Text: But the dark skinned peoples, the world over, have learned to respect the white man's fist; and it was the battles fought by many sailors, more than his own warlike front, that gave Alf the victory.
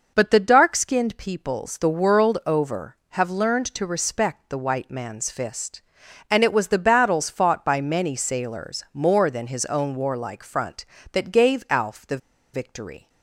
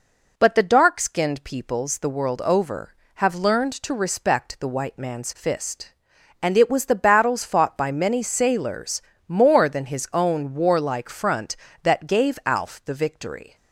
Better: second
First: pauses between "the" and "victory"; at 12.1 s; 0.36 s long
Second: none

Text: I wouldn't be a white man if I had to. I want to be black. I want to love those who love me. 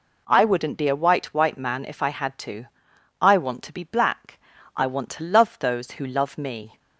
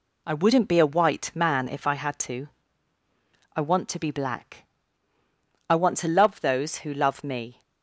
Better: second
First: says "white" twice; at 1.3 s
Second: none

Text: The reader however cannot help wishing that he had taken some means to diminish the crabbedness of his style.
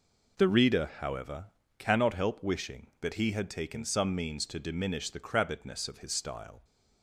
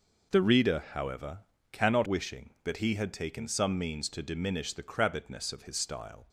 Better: first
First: pauses between "however" and "cannot"; slight; at 1.4 s; 0.32 s long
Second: pauses between "however" and "cannot"; slight; at 1.3 s; 0.32 s long // skips "help"; at 2.0 s

